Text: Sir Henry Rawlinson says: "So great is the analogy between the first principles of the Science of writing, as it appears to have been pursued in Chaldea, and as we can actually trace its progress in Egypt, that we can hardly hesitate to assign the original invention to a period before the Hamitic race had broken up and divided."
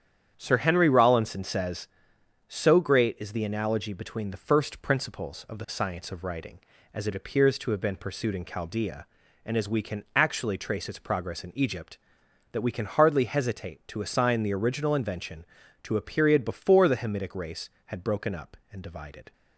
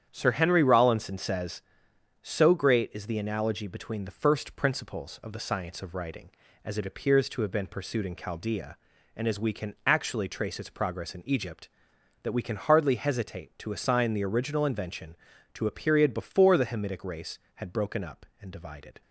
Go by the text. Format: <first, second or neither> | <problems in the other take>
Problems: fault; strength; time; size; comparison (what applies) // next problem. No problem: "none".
neither | starts louder than the rest; strong; the same in both